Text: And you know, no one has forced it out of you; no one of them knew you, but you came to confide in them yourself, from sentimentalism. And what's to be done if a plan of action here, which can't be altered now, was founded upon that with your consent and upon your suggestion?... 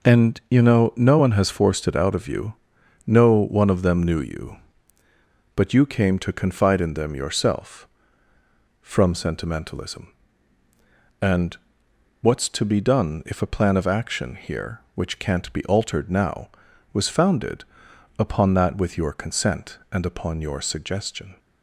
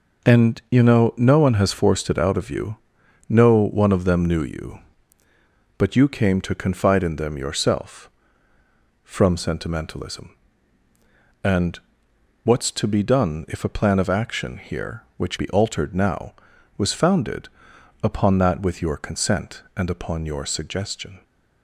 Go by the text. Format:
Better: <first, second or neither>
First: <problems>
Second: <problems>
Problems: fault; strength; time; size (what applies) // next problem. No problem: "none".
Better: first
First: pauses between "And" and "what's"; noticeable; at 11.5 s; 0.66 s long // pauses between "founded" and "upon"; noticeable; at 17.6 s; 0.56 s long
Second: pauses between "And" and "what's"; noticeable; at 11.7 s; 0.66 s long // skips "can't"; at 15.3 s // pauses between "founded" and "upon"; noticeable; at 17.4 s; 0.56 s long